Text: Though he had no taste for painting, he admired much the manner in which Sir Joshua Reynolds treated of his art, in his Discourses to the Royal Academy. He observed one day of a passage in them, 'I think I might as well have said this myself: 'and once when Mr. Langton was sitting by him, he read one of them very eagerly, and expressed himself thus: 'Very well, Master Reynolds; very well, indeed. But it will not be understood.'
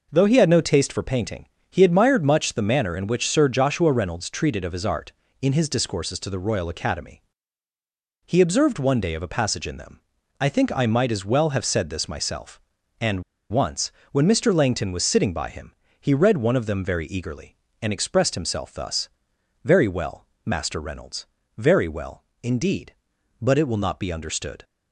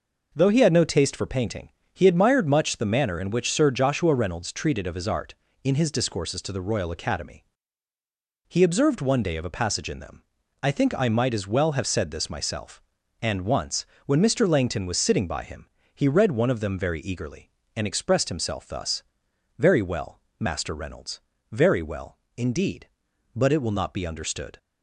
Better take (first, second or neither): second